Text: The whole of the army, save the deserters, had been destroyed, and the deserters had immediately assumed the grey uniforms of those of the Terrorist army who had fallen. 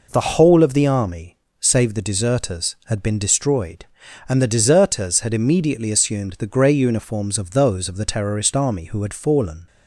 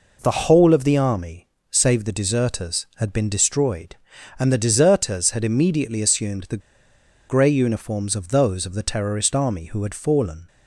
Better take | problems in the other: first | pauses between "the" and "grey"; noticeable; at 6.5 s; 0.68 s long

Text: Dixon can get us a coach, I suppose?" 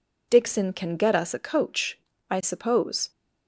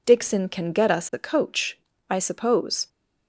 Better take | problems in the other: neither | none

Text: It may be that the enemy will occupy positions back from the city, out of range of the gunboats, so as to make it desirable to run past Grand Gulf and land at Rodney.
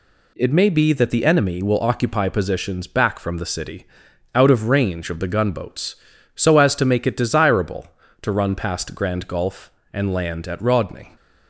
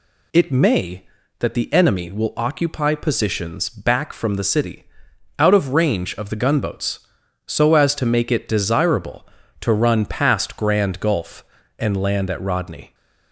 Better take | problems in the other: first | skips "be"; at 1.2 s

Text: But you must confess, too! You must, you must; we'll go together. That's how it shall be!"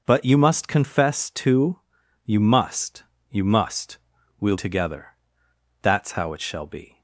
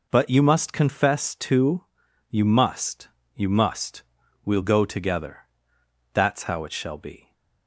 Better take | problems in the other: second | skips "go"; at 4.5 s

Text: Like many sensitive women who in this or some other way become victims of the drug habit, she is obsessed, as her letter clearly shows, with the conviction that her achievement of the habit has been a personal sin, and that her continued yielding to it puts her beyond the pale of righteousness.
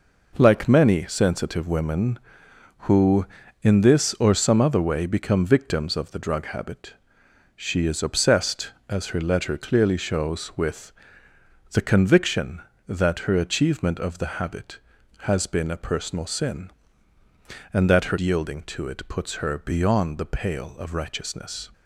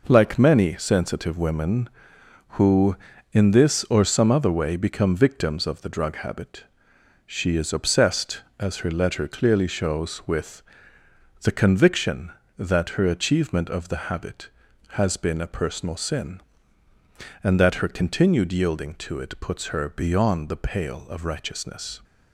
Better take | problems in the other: second | pauses between "with" and "the"; noticeable; at 10.9 s; 0.80 s long; noticeable in the second // skips "continued"; at 18.1 s

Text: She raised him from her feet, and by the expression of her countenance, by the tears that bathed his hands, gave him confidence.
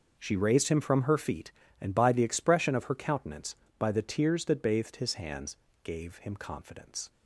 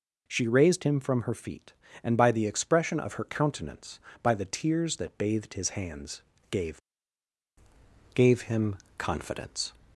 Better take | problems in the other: first | says "gave" twice; at 8.1 s // pauses between "him" and "confidence"; slight; at 8.7 s; 0.20 s long

